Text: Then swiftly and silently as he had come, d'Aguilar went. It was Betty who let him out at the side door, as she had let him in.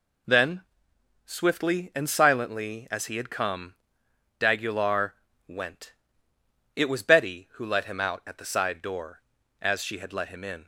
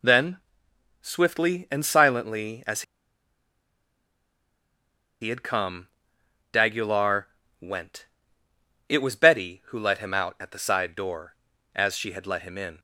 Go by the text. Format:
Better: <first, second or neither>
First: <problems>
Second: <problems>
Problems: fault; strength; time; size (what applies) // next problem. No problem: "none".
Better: first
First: pauses between "Then" and "swiftly"; noticeable; at 0.6 s; 0.64 s long // pauses between "d'Aguilar" and "went"; slight; at 5.1 s; 0.34 s long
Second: pauses between "Then" and "swiftly"; noticeable; at 0.3 s; 0.64 s long // pauses between "as" and "he"; strong; at 2.8 s; 2.3 s long // pauses between "d'Aguilar" and "went"; slight; at 7.2 s; 0.34 s long